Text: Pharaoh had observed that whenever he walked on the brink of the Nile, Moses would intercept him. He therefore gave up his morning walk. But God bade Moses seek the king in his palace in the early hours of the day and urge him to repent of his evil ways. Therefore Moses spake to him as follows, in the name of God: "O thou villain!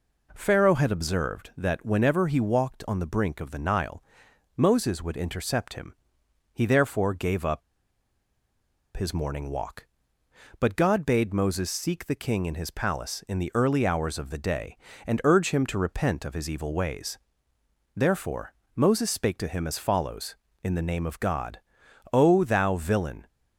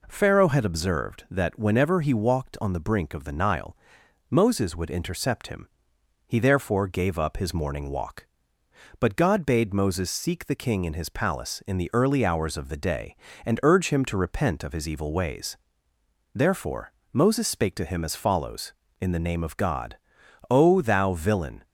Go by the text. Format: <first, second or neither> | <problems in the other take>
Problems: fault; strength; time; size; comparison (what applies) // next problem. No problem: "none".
second | pauses between "up" and "his"; strong; at 7.6 s; 1.3 s long // pauses between "Therefore" and "Moses"; slight; at 18.5 s; 0.22 s long; slight in the second